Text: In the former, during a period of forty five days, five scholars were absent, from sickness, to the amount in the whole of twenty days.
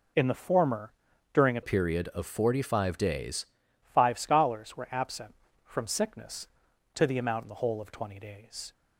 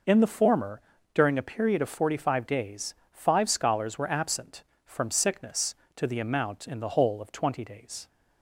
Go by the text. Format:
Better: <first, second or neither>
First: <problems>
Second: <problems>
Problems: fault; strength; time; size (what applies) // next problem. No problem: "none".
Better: second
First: changes voice from "period" to "days"; from 1.6 to 3.4 s; 1.8 s long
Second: none